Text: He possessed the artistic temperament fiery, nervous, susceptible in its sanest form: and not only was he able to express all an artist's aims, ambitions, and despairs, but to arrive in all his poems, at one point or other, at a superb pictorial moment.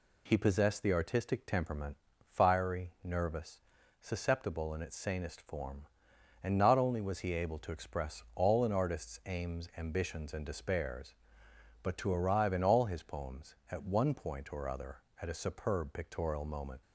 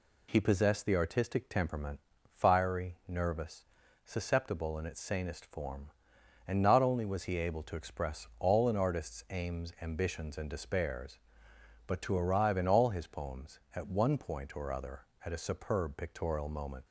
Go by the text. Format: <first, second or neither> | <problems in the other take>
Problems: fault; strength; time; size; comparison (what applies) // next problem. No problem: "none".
neither | pauses between "temperament" and "fiery"; the same in both